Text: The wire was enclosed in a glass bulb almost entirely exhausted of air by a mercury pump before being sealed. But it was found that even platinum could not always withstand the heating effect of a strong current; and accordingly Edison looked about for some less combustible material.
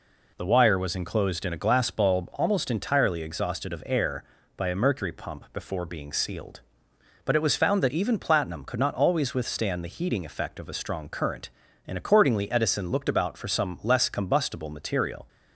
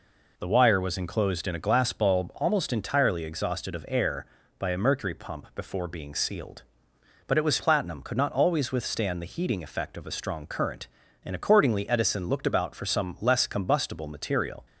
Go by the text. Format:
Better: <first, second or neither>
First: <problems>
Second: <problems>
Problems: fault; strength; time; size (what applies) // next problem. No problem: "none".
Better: first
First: none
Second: skips "found that even"; at 7.5 s